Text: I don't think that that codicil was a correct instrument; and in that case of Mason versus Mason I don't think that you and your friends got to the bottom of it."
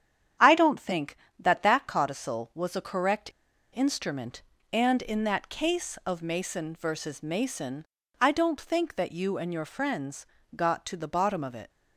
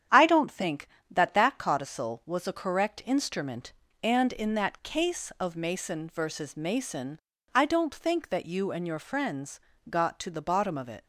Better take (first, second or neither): second